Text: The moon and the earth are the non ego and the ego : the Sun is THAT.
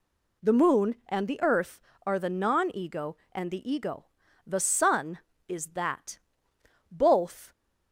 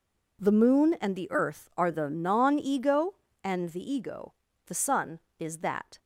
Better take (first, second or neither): second